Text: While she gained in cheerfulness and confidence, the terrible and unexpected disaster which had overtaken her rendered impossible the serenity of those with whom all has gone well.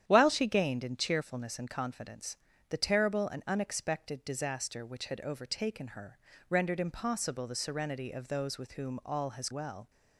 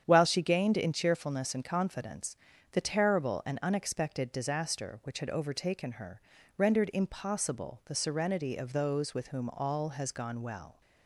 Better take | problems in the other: second | starts louder than the rest; strong; until 1.0 s; 10 dB; strong in the second // pauses between "her" and "rendered"; slight; at 6.1 s; 0.28 s long; also in the second // skips "gone"; at 9.5 s

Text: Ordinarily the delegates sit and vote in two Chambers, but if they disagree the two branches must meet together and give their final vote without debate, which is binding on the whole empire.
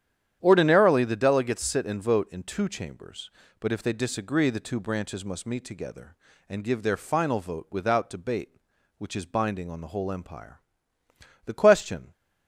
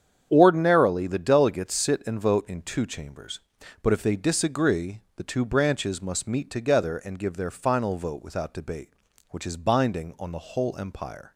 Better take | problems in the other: second | starts louder than the rest; strong; until 1.4 s; 10 dB; strong in the second // goes on to say "The question"; noticeable; from 11.4 s on; 0.66 s long

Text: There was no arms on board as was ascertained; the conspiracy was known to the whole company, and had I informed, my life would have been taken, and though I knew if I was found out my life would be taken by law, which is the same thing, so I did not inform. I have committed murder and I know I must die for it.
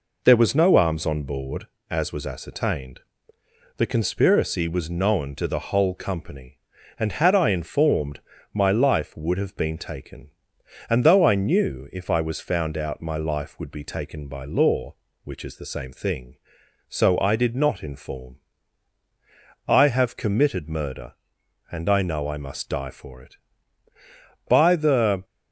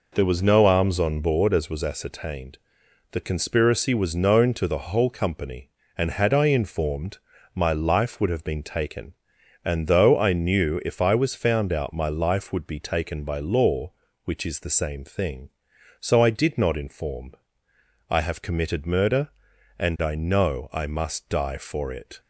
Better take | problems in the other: second | goes on to say "By the"; noticeable; from 24.4 s on; 0.76 s long

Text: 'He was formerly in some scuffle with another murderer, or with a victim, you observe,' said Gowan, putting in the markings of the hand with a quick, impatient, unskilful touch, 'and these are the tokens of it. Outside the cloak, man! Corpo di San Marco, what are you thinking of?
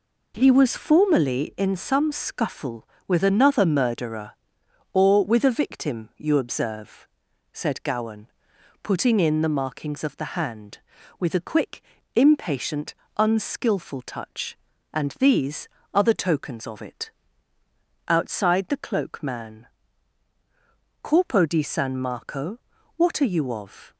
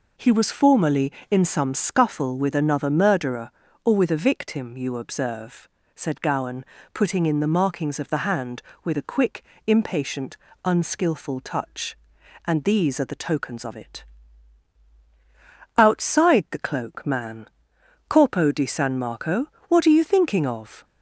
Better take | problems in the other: second | skips "thinking"; at 23.5 s

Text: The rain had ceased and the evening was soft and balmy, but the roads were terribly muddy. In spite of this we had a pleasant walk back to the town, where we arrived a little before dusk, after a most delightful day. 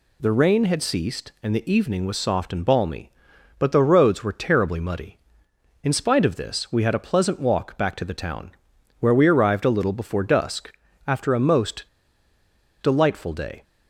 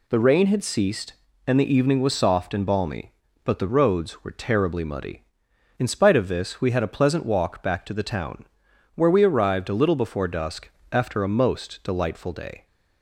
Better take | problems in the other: second | pauses between "most" and "delightful"; noticeable; at 11.8 s; 0.95 s long

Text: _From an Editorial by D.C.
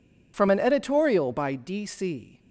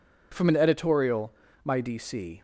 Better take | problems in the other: first | says "my" for "by"; at 1.6 s

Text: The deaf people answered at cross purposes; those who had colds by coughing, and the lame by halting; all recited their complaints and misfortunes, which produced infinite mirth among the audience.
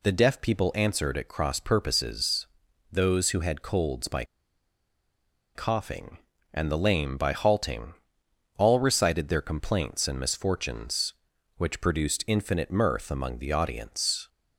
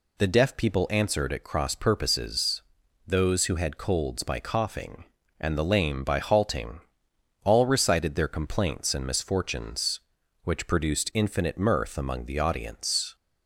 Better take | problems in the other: second | pauses between "by" and "coughing"; strong; at 4.2 s; 1.3 s long

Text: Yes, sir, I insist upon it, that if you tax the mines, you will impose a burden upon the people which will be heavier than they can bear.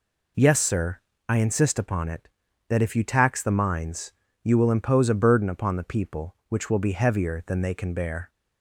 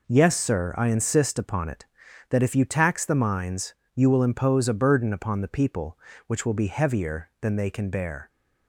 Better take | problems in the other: neither | none

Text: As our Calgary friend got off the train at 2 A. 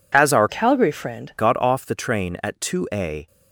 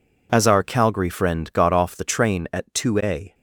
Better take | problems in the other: second | changes voice from "Calgary" to "friend"; from 0.4 to 1.3 s; 0.9 s long

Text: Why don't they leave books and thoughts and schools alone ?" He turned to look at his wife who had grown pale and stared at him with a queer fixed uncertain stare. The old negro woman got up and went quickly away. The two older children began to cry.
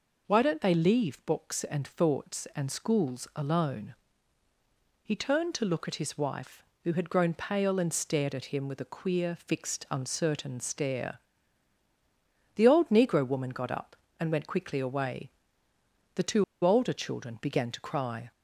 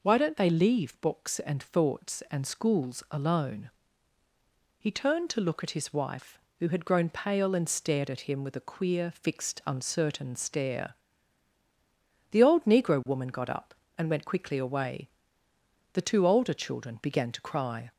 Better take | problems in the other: second | pauses between "two" and "older"; slight; at 16.4 s; 0.20 s long

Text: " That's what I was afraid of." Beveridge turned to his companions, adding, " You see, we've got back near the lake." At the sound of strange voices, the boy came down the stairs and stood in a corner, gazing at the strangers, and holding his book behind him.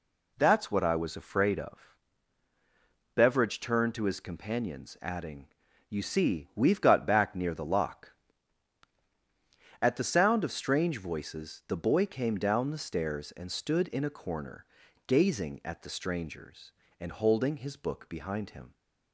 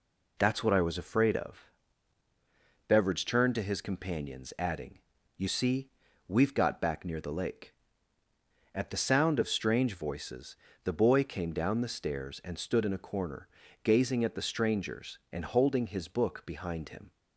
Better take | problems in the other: second | says "lock" for "lake"; at 7.6 s

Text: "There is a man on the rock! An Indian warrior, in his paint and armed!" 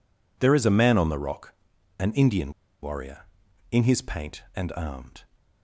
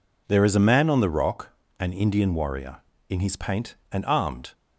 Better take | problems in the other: second | pauses between "Indian" and "warrior"; slight; at 2.5 s; 0.30 s long

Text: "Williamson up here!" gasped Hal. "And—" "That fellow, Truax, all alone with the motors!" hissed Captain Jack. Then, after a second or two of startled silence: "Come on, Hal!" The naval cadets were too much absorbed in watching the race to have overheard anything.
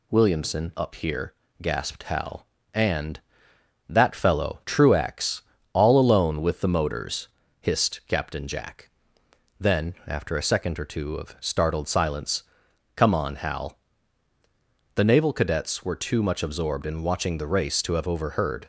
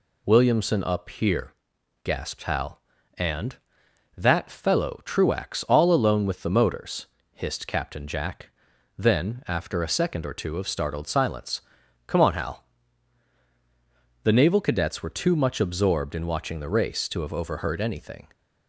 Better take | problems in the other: second | stops before "anything"; at 18.6 s

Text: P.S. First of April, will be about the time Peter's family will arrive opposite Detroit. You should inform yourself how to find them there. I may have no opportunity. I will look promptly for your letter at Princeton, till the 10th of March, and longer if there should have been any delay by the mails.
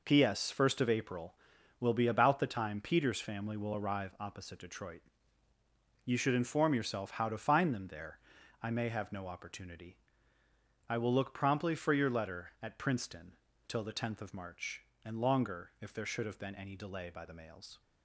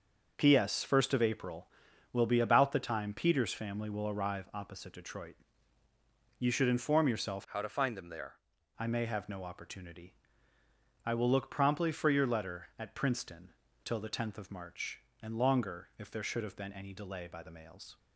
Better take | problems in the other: first | starts louder than the rest; noticeable; until 1.3 s; 6 dB // changes voice from "how" to "there"; from 7.4 to 8.3 s; 0.9 s long

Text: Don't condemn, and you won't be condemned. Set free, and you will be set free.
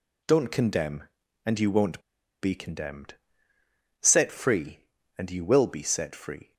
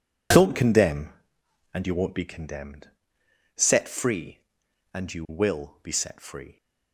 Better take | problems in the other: second | pauses between "won't" and "be"; at 1.9 s; 0.42 s long

